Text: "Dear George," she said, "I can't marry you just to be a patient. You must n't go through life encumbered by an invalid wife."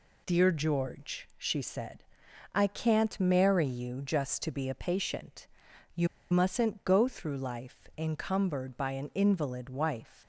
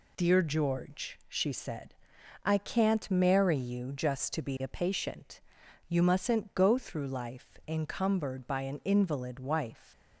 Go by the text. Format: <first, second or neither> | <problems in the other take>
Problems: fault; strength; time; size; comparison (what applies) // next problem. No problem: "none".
second | pauses between "You" and "must"; slight; at 6.0 s; 0.24 s long